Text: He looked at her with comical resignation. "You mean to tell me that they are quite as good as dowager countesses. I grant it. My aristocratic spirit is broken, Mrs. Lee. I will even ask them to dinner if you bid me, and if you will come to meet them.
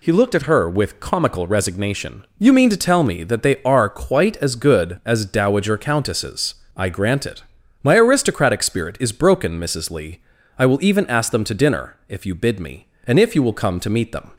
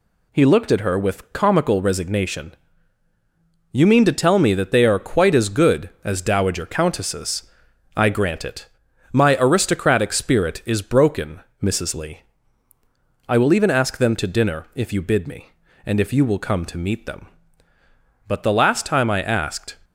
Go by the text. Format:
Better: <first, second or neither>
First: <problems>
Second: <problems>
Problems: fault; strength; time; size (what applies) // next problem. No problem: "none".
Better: first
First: none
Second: goes on to say "But the last time I asked"; from 18.2 s on; 1.5 s long